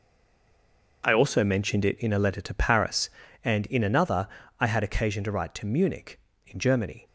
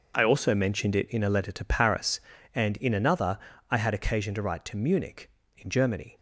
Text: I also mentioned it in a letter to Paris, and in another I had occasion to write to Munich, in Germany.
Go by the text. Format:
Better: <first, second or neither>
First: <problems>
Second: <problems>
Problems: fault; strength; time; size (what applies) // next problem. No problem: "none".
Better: second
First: stays silent before the first word; until 1.0 s; 1.0 s long // pauses between "another" and "I"; slight; at 4.2 s; 0.32 s long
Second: pauses between "another" and "I"; slight; at 3.3 s; 0.32 s long